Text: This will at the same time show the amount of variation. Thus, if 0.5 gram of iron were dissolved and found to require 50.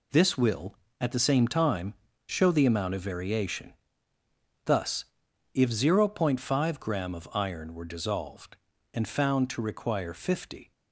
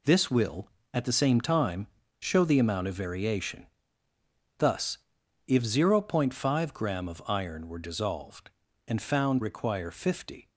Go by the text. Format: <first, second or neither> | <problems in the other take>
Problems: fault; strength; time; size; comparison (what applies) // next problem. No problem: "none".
first | pauses between "time" and "show"; slight; at 1.8 s; 0.32 s long; slight in the first // skips "to"; at 9.4 s